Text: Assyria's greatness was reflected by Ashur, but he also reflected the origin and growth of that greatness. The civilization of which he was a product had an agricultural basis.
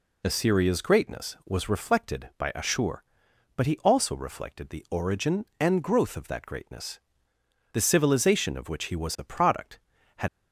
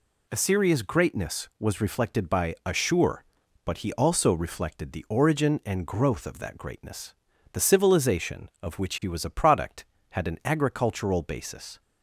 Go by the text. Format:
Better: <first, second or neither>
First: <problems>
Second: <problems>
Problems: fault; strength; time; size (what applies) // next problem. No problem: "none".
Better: second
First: stops before "an agricultural basis"; at 10.2 s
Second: none